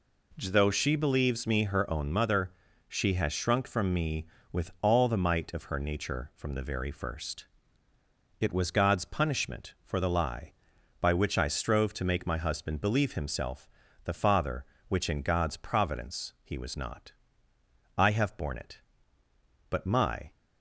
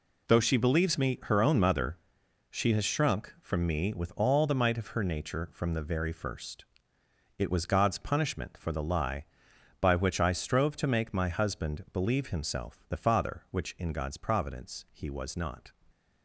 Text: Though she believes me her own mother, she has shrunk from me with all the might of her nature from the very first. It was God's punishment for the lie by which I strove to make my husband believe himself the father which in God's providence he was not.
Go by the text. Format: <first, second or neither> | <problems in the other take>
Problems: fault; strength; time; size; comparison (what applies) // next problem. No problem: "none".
second | pauses between "himself" and "the"; slight; at 13.6 s; 0.36 s long // goes on to say "I have borne it but my"; strong; from 17.9 s on; 2.3 s long